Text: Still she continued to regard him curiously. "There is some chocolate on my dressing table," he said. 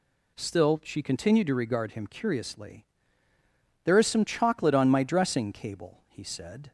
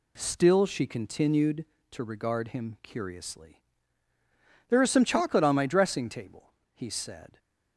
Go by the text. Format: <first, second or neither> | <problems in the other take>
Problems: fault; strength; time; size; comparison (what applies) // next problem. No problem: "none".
second | says "cable" for "table"; at 5.5 s